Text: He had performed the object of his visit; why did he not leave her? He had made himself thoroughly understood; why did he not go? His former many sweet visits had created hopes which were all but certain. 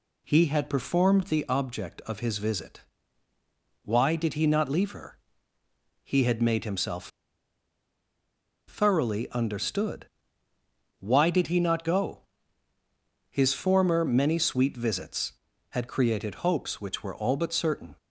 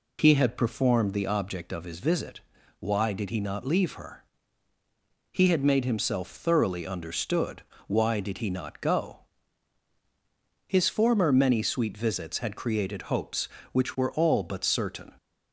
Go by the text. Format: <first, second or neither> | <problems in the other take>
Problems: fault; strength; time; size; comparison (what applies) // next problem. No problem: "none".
second | pauses between "himself" and "thoroughly"; strong; at 7.0 s; 1.6 s long